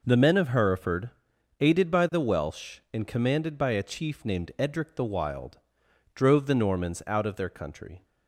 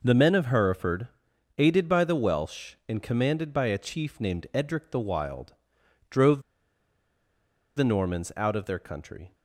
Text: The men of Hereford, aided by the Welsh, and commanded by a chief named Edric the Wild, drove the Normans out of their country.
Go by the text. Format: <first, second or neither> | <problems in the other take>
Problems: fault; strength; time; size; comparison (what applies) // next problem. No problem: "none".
first | pauses between "drove" and "the"; strong; at 6.4 s; 1.3 s long